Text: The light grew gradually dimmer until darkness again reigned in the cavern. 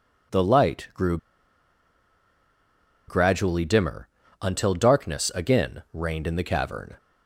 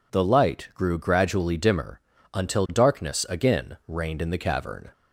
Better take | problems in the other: second | pauses between "grew" and "gradually"; strong; at 1.1 s; 1.9 s long // pauses between "dimmer" and "until"; slight; at 4.0 s; 0.32 s long; slight in the second

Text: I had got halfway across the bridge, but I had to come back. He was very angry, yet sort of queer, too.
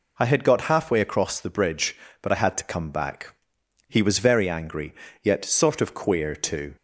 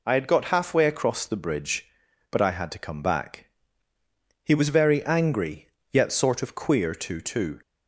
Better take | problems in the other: first | says "too" twice; at 7.2 s

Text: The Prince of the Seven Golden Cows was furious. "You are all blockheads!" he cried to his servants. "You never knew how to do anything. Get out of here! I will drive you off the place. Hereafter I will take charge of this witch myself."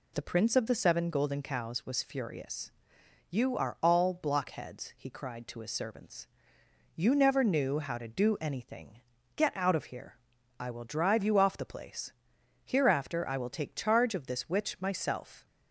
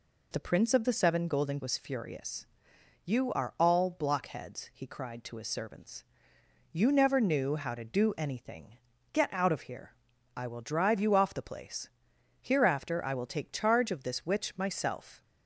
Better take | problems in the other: first | skips "Cows"; at 1.5 s

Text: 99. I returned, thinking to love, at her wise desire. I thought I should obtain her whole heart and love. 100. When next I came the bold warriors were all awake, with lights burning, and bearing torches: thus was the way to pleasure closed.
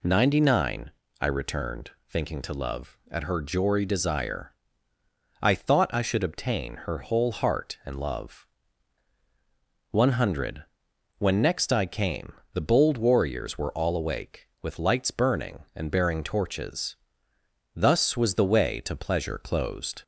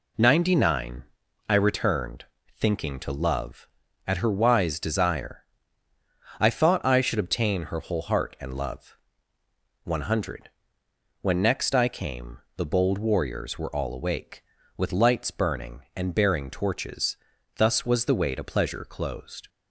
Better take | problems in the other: second | says "jory" for "wise"; at 3.4 s // pauses between "came" and "the"; slight; at 12.3 s; 0.22 s long; slight in the second

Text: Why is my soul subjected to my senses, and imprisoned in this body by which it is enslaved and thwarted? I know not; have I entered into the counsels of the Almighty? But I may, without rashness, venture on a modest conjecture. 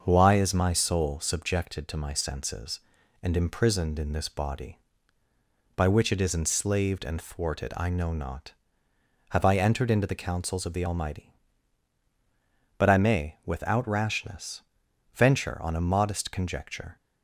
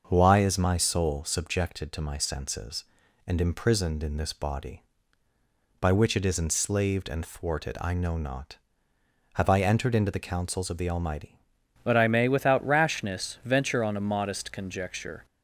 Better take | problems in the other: first | starts louder than the rest; until 1.0 s; 6.5 dB; also in the first // changes voice at "But"; from 11.8 s on; 3.4 s long

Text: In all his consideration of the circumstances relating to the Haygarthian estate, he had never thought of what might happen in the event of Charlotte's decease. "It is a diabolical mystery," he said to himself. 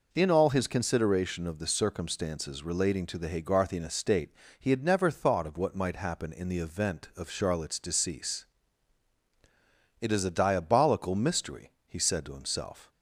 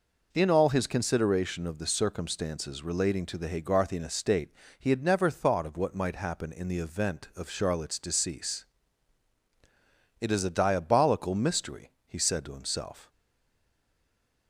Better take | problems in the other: first | stays silent after the last word; noticeable; from 13.1 s on; 1.3 s long

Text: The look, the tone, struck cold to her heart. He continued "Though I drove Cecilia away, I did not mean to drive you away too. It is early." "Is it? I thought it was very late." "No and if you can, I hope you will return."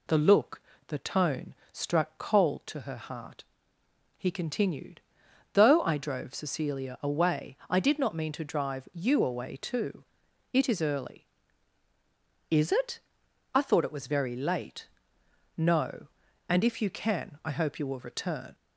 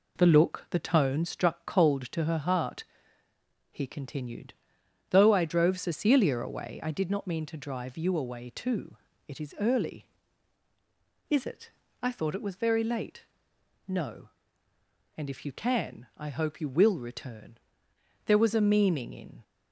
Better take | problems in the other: first | pauses between "continued" and "Though"; noticeable; at 4.5 s; 0.56 s long; noticeable in the first // goes on to say "There was a meaning in"; noticeable; from 18.2 s on; 1.1 s long

